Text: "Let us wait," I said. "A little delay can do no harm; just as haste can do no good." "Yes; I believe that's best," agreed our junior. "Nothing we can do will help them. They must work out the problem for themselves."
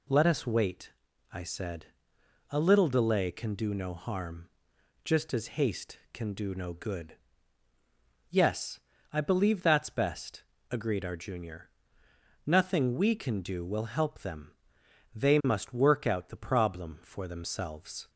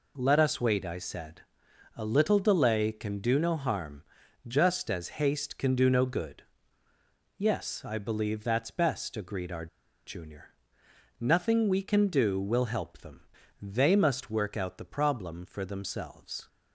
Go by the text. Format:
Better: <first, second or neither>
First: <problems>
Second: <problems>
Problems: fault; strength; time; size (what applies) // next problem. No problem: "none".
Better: first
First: none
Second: pauses between "our" and "junior"; at 9.6 s; 0.40 s long